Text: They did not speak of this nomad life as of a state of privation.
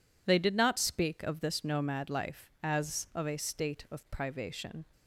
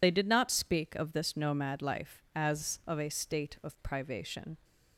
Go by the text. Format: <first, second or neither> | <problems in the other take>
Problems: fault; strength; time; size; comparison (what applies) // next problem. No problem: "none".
first | loses the start of "They"; at 0.0 s; 50 ms